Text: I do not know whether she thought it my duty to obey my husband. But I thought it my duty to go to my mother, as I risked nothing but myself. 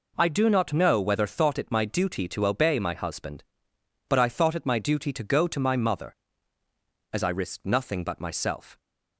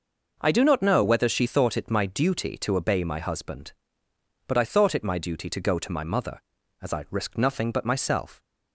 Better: second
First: skips "she"; at 1.2 s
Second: none

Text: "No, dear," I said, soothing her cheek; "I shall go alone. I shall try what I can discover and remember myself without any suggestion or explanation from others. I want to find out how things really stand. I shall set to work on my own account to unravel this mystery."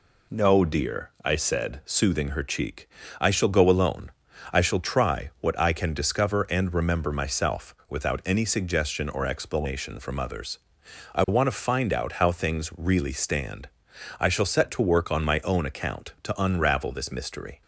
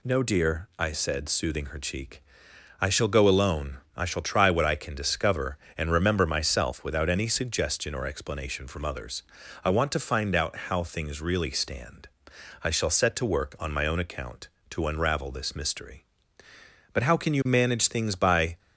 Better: first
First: none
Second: goes on to say "But how can you manage things by"; from 16.9 s on; 1.6 s long

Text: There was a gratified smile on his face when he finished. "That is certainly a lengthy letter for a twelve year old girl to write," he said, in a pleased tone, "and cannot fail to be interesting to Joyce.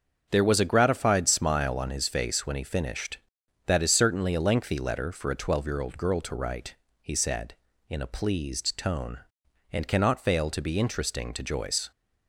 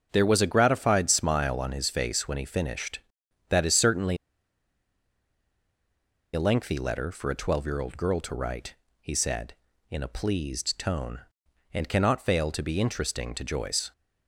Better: first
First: starts louder than the rest; until 1.3 s; 7 dB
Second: starts louder than the rest; strong; until 1.1 s; 7 dB // pauses between "certainly" and "a"; strong; at 4.1 s; 2.1 s long

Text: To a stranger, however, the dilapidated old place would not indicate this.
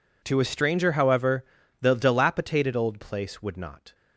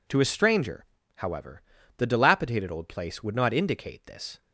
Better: second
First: stops before "indicate this"; at 3.9 s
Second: none

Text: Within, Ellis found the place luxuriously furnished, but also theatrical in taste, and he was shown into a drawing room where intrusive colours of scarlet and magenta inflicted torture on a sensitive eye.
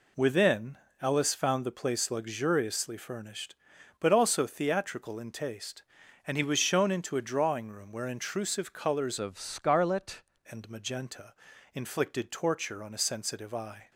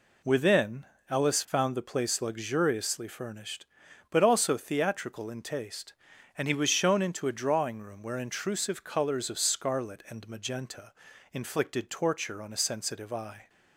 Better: second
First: changes voice from "of" to "scarlet"; from 9.1 to 10.2 s; 1.1 s long // pauses between "magenta" and "inflicted"; at 11.3 s; 0.40 s long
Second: pauses between "magenta" and "inflicted"; at 10.9 s; 0.40 s long

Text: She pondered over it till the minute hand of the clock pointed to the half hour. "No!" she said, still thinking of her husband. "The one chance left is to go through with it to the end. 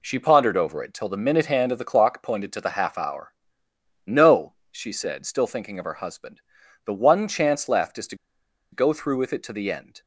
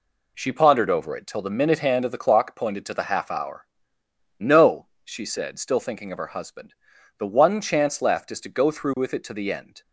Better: second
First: pauses between "to" and "go"; noticeable; at 8.1 s; 0.56 s long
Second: none

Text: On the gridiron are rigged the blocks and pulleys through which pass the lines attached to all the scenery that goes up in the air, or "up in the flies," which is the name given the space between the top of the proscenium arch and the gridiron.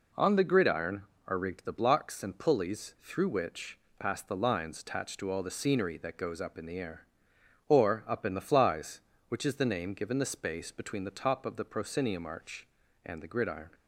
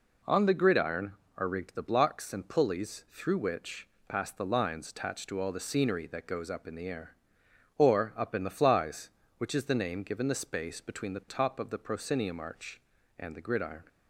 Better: neither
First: pauses between "which" and "pass"; slight; at 3.7 s; 0.18 s long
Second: pauses between "which" and "pass"; slight; at 3.8 s; 0.18 s long

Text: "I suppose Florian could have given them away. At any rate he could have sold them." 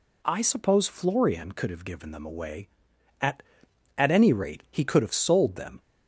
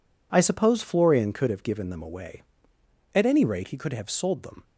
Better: second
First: says "At" twice; at 3.9 s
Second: none

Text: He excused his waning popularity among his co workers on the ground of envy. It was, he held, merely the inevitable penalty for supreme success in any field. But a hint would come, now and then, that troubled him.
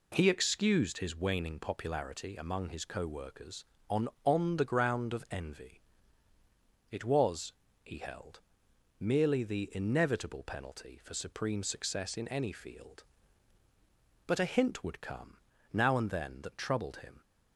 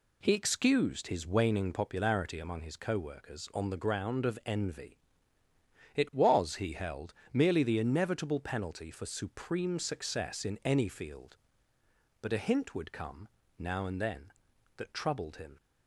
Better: second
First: says "on" twice; at 4.2 s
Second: none

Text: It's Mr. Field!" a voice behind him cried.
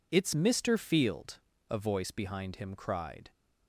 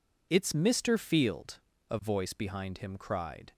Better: neither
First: none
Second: none

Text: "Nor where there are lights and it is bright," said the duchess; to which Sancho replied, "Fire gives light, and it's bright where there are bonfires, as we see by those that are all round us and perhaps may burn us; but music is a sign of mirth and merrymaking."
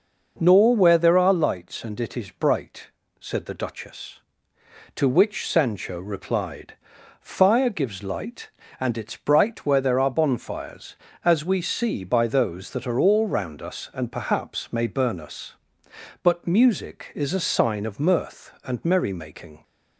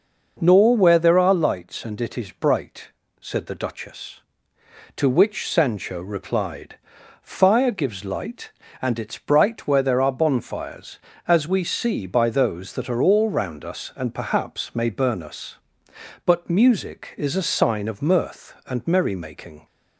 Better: neither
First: none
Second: none

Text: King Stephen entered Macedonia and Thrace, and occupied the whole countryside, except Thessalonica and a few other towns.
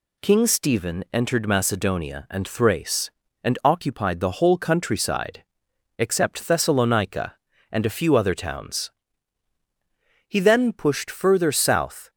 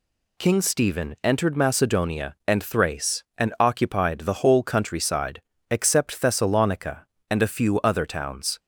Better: second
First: goes on to say "He then pushed further south"; strong; from 10.2 s on; 1.8 s long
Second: none

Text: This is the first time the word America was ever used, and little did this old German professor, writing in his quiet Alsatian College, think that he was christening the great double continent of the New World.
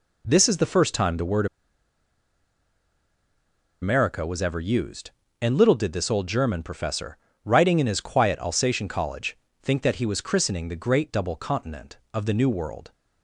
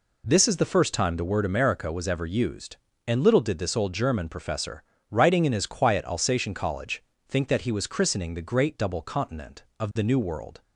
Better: second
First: pauses between "word" and "America"; strong; at 1.4 s; 2.3 s long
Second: none

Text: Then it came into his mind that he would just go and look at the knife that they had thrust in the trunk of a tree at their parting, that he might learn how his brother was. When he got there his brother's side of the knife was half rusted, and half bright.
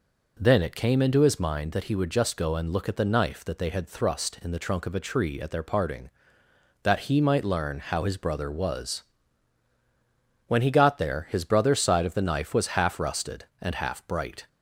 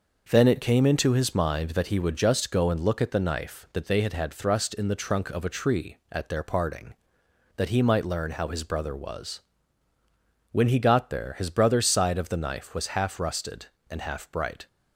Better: first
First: none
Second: says "had" twice; at 4.1 s

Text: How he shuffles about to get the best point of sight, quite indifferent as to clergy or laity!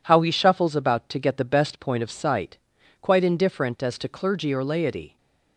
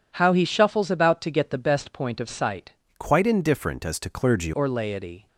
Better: first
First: none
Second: changes voice from "quite" to "clergy"; from 2.9 to 4.5 s; 1.6 s long

